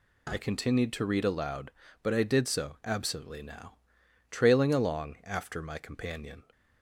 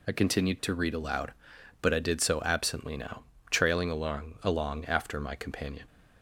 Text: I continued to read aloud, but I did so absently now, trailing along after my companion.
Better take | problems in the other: first | says "along" twice; at 4.4 s

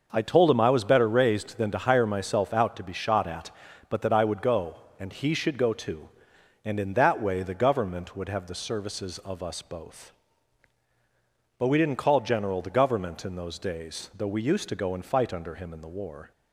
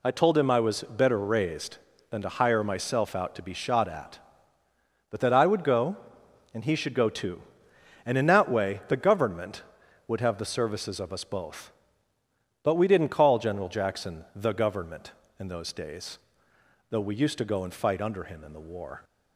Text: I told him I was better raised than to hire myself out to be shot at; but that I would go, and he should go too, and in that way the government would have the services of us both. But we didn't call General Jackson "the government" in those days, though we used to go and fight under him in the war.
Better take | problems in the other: second | skips "Jackson"; at 12.6 s

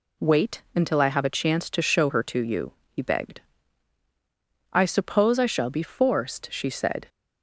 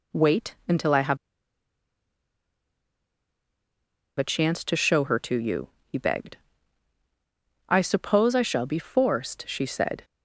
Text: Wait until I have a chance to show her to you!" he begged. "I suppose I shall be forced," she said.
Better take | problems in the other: first | pauses between "have" and "a"; strong; at 1.1 s; 3.0 s long

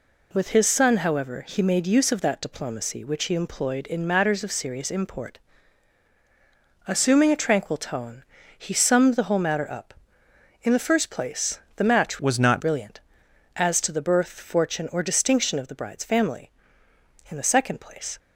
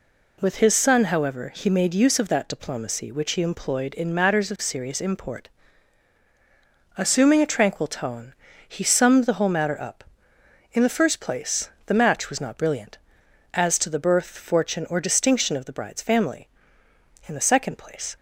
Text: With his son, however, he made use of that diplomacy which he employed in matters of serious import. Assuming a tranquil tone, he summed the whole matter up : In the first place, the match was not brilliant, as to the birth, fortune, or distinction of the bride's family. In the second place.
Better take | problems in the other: second | changes voice from "was" to "not"; from 12.1 to 12.6 s; 0.5 s long

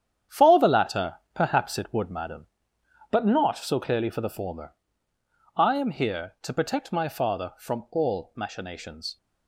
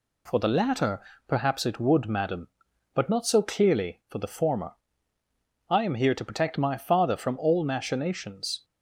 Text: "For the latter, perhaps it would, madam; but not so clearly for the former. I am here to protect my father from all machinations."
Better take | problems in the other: second | gets quieter; strong; throughout; 9 dB

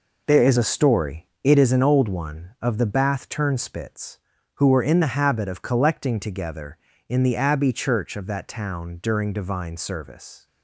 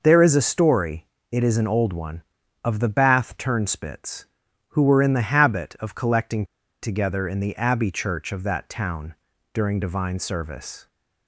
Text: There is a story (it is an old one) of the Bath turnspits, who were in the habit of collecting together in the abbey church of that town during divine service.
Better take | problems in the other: first | pauses between "collecting" and "together"; at 6.4 s; 0.37 s long // pauses between "town" and "during"; at 9.1 s; 0.40 s long

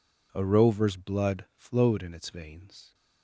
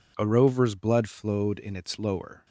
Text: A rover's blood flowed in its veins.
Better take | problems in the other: first | says "lower" for "veins"; at 1.9 s

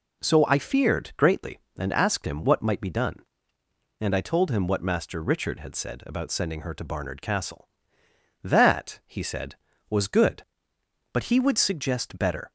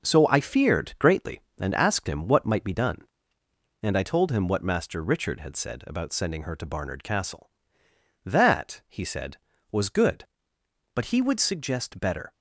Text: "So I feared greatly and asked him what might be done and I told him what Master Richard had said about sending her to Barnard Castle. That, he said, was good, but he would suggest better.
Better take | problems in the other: first | gets quieter; throughout; 6.5 dB

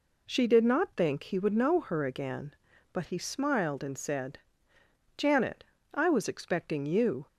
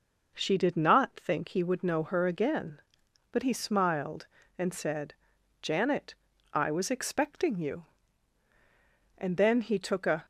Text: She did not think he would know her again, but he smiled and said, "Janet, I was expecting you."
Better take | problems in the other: first | goes on to say "And then he took a"; noticeable; from 9.1 s on; 1.1 s long

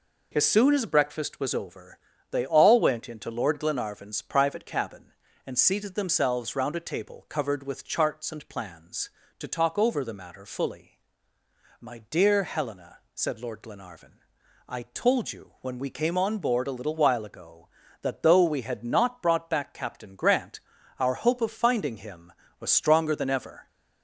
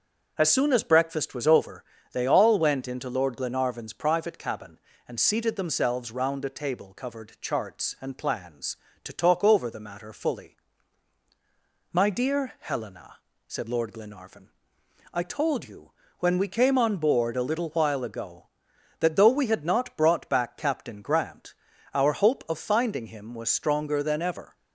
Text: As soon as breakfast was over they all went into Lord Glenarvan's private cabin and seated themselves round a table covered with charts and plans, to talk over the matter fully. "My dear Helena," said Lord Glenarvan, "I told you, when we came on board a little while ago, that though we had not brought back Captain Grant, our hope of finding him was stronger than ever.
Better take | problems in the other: first | pauses between "over" and "they"; slight; at 1.8 s; 0.28 s long; slight in the first // skips "with"; at 7.3 s

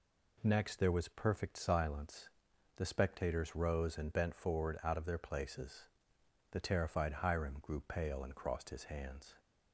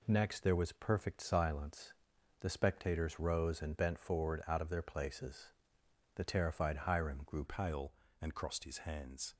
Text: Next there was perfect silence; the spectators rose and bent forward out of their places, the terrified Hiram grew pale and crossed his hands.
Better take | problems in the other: first | changes voice at "pale"; from 7.4 s on; 1.9 s long

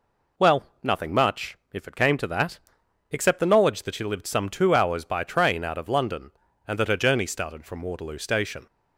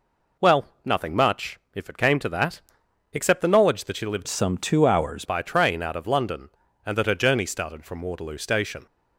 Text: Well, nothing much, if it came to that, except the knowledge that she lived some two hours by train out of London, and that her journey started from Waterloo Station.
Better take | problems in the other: first | changes voice from "some" to "hours"; from 4.2 to 5.2 s; 1.0 s long

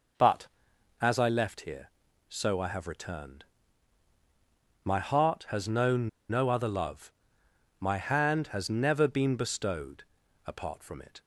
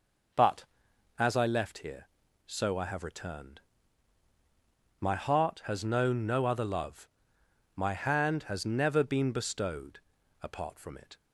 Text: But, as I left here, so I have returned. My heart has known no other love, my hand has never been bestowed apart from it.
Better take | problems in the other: second | pauses between "known" and "no"; slight; at 6.0 s; 0.20 s long // pauses between "bestowed" and "apart"; at 10.0 s; 0.42 s long; also in the second

